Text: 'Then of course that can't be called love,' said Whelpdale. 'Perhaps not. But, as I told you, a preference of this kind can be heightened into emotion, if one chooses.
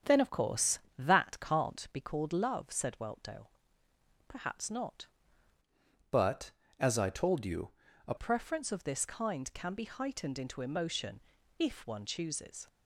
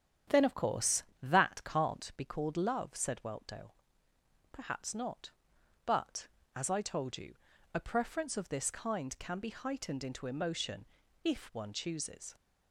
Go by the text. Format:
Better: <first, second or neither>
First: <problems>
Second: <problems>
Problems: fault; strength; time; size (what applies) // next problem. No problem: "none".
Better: second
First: starts louder than the rest; strong; until 1.2 s; 8 dB // changes voice from "But" to "a"; from 6.1 to 8.1 s; 2.0 s long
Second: starts louder than the rest; strong; until 1.4 s; 9 dB